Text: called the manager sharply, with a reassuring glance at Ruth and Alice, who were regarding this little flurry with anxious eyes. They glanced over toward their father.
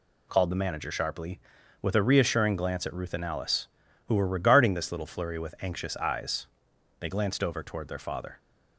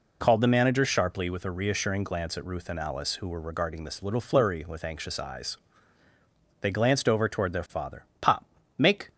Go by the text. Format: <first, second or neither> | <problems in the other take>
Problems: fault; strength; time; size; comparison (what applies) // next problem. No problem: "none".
first | goes on to say "Pop make"; noticeable; from 8.2 s on; 0.90 s long